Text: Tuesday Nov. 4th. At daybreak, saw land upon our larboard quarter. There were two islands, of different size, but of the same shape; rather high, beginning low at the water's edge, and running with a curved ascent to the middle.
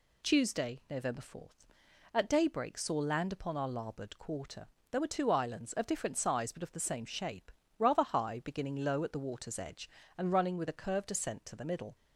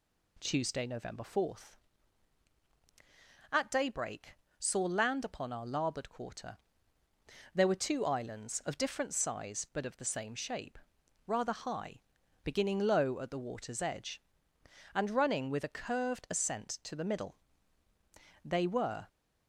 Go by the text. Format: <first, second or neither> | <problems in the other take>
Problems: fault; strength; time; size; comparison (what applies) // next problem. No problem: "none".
first | goes on to say "They were"; noticeable; from 18.4 s on; 0.62 s long